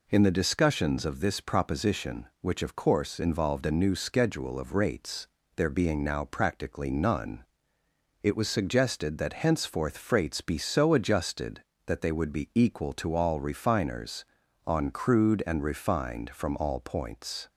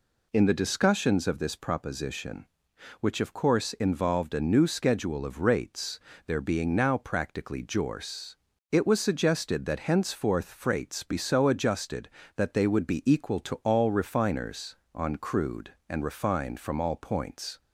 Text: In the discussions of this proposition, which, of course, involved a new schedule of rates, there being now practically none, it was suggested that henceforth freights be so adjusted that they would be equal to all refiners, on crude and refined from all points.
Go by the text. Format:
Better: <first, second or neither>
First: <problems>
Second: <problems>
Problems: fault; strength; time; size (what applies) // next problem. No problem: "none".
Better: first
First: none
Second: says "jorce" for "none"; at 7.6 s